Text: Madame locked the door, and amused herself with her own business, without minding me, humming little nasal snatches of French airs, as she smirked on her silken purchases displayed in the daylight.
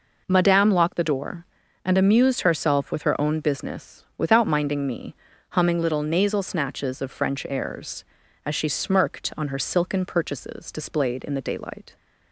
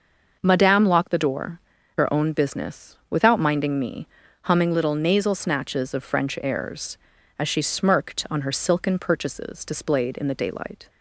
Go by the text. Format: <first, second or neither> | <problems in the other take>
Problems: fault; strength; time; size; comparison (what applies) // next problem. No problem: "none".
first | starts louder than the rest; noticeable; until 1.4 s; 6 dB // skips "and amused herself with"; at 1.7 s